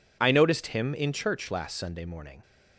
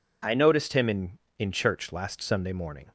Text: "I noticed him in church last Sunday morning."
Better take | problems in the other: first | says "in" twice; at 1.3 s

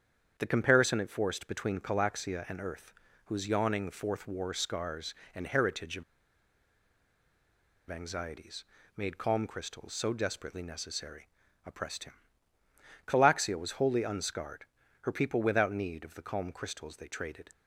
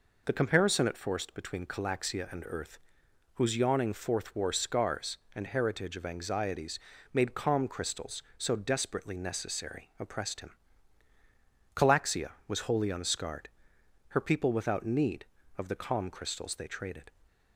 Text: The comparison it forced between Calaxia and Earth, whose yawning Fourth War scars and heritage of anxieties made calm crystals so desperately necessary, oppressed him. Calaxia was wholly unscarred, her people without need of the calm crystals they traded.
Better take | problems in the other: second | starts louder than the rest; strong; until 1.3 s; 8 dB // pauses between "of" and "anxieties"; strong; at 6.0 s; 1.8 s long // pauses between "anxieties" and "made"; slight; at 8.6 s; 0.32 s long; slight in the second

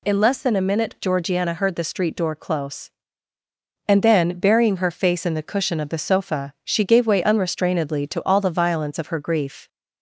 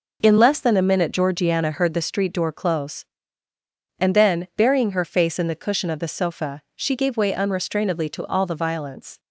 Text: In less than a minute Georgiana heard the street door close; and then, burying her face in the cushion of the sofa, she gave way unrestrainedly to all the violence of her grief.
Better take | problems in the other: first | stops before "of her grief"; at 9.1 s

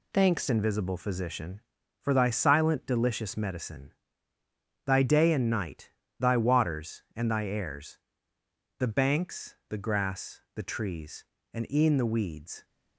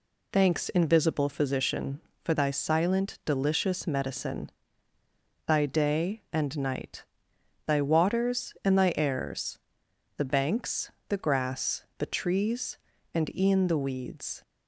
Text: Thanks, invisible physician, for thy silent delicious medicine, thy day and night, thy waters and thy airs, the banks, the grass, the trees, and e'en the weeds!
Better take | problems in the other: second | changes voice at "invisible"; from 0.4 s on; 12.2 s long

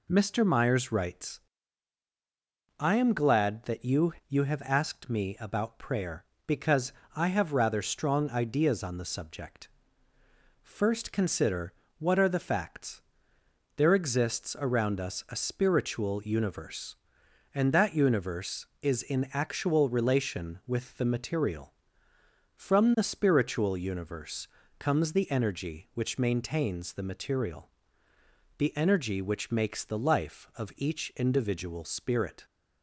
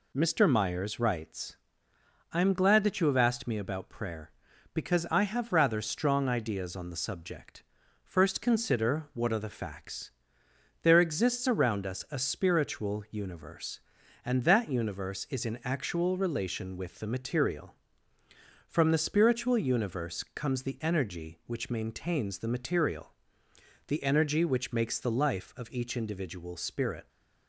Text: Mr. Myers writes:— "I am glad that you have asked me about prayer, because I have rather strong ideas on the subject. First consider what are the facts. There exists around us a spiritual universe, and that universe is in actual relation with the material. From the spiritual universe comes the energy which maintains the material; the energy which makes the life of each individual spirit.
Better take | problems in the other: second | says "you" twice; at 4.2 s // pauses between "because" and "I"; slight; at 6.9 s; 0.22 s long // pauses between "consider" and "what"; slight; at 11.7 s; 0.26 s long // pauses between "universe" and "comes"; slight; at 24.4 s; 0.28 s long

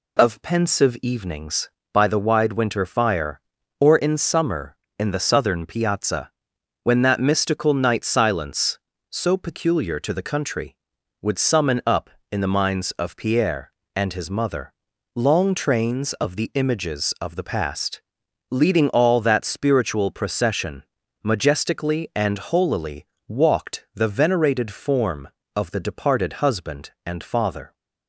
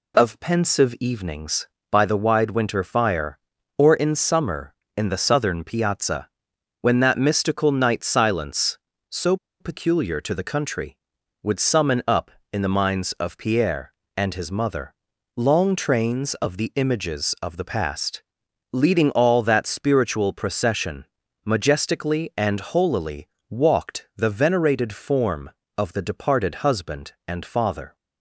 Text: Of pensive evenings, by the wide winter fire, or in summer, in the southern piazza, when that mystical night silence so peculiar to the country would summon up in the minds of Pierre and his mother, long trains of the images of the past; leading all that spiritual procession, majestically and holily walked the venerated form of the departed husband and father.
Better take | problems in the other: first | pauses between "so" and "peculiar"; slight; at 9.3 s; 0.24 s long // pauses between "holily" and "walked"; slight; at 23.2 s; 0.24 s long; slight in the first

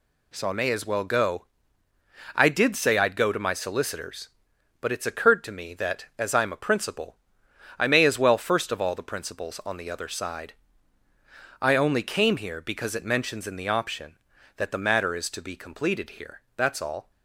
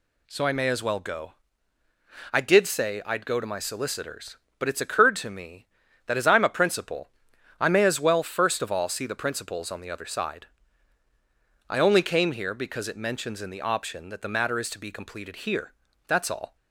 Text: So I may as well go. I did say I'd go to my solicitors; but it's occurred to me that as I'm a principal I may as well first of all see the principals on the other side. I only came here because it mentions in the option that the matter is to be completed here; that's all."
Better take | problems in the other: second | pauses between "principal" and "I"; noticeable; at 7.1 s; 0.62 s long; noticeable in the second // skips "see"; at 8.9 s

